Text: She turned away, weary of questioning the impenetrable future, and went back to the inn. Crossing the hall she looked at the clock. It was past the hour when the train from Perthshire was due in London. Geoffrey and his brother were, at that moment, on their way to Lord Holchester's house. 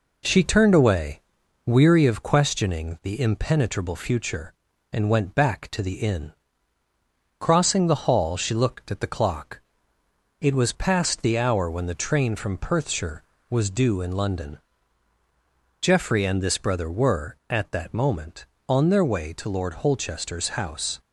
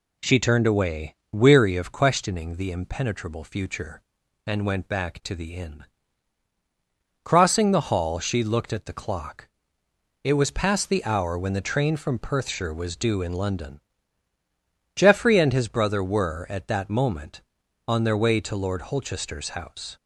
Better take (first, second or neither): second